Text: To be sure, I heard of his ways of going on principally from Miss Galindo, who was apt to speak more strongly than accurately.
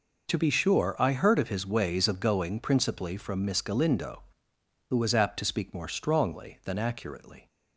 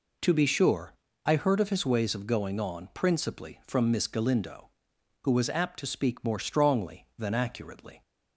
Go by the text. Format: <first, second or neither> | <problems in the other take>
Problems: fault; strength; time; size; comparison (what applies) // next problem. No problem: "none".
second | skips "on"; at 2.5 s